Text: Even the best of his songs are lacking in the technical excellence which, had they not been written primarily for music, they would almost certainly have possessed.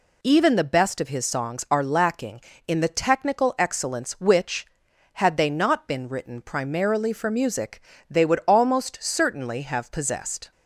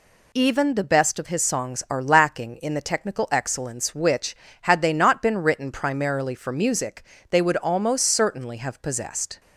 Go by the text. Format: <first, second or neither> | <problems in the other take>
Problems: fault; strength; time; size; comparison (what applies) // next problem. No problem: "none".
neither | none